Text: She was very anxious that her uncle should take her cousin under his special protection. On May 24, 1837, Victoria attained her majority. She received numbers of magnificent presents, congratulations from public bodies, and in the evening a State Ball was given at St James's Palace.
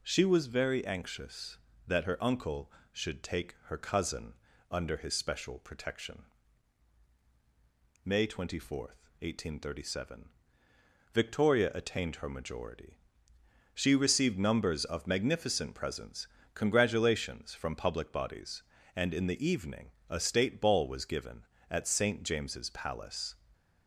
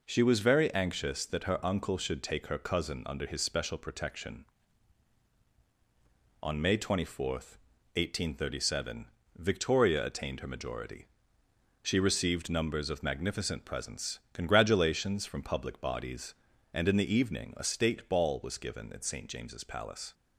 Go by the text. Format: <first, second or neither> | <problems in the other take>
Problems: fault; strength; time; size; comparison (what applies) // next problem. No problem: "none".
second | pauses between "cousin" and "under"; slight; at 4.3 s; 0.36 s long // skips "On"; at 7.1 s // pauses between "evening" and "a"; slight; at 19.9 s; 0.18 s long